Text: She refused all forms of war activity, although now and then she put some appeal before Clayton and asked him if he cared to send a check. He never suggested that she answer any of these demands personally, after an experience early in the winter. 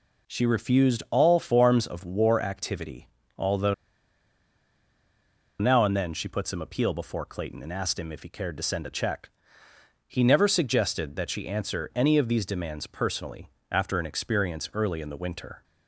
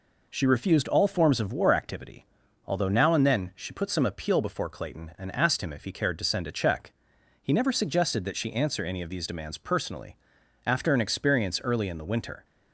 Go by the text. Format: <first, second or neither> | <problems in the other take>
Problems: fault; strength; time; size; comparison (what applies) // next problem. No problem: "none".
second | pauses between "although" and "now"; strong; at 3.7 s; 1.8 s long